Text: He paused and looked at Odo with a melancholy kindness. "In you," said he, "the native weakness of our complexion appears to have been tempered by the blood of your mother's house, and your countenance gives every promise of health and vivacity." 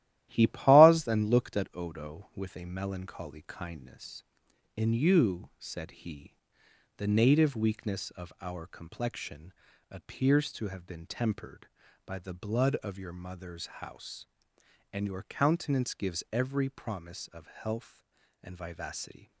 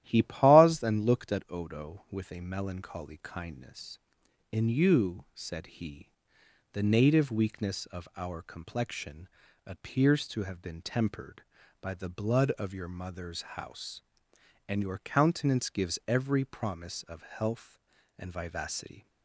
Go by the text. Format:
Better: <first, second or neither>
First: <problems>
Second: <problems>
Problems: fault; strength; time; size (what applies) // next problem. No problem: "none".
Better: second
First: gets quieter; noticeable; throughout; 5.5 dB // starts louder than the rest; strong; until 1.3 s; 14 dB // pauses between "complexion" and "appears"; slight; at 9.5 s; 0.36 s long // pauses between "mother's" and "house"; slight; at 13.6 s; 0.16 s long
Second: starts louder than the rest; strong; until 1.0 s; 13 dB // pauses between "complexion" and "appears"; slight; at 9.2 s; 0.36 s long // pauses between "mother's" and "house"; slight; at 13.4 s; 0.16 s long